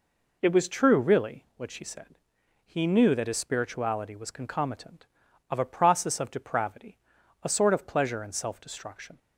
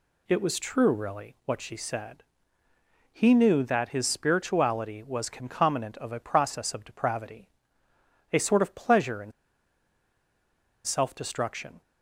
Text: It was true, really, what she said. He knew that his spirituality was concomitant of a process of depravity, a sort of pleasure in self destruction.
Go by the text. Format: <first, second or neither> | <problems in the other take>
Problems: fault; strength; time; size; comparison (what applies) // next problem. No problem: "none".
first | pauses between "in" and "self"; strong; at 9.3 s; 1.5 s long